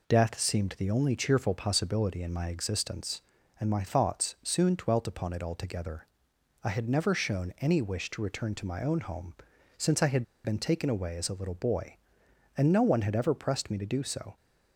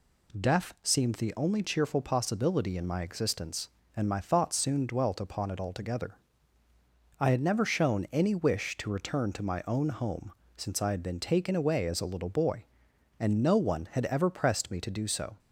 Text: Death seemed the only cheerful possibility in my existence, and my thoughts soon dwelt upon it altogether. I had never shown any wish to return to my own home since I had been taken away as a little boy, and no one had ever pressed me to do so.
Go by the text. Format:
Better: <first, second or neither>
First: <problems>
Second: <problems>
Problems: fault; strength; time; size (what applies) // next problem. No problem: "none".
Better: second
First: pauses between "home" and "since"; noticeable; at 9.3 s; 0.46 s long // pauses between "had" and "been"; slight; at 10.2 s; 0.21 s long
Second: pauses between "home" and "since"; slight; at 10.3 s; 0.24 s long